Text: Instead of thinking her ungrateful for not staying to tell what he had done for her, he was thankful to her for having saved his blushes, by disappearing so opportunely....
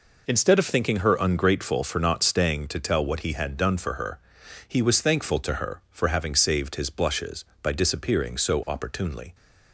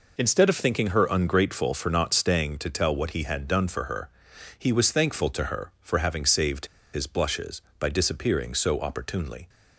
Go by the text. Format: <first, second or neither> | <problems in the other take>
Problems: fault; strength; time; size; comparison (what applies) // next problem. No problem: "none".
first | pauses between "saved" and "his"; slight; at 6.6 s; 0.27 s long